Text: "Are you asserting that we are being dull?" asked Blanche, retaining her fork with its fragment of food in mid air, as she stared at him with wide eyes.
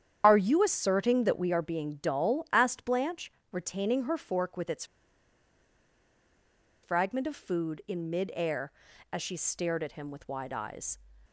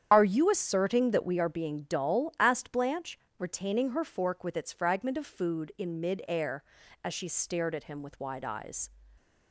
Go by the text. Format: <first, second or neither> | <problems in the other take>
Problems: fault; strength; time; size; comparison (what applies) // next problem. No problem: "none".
second | starts louder than the rest; strong; until 1.2 s; 8.5 dB; strong in the second // pauses between "its" and "fragment"; strong; at 4.8 s; 1.9 s long